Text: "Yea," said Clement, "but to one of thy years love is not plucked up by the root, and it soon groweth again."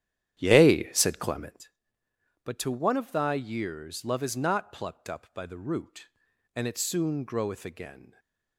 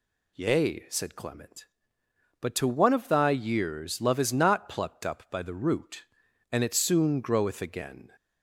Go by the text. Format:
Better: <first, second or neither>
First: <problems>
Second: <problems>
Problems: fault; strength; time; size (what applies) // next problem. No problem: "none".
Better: second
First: starts louder than the rest; strong; until 1.6 s; 11 dB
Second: none